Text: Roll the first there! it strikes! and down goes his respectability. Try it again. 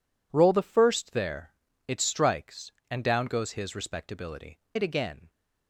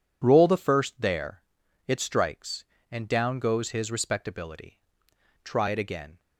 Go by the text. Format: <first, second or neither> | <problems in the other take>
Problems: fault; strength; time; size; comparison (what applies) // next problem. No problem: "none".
second | skips "Try"; at 4.6 s